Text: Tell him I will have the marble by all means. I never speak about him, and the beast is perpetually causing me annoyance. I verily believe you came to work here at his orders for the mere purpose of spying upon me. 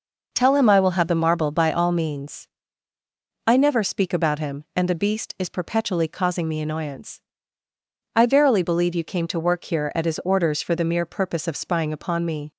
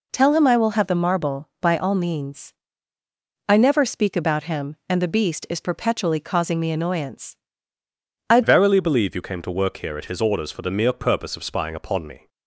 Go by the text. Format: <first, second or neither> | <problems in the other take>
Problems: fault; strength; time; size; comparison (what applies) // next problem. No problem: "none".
first | changes voice at "verily"; from 8.4 s on; 3.8 s long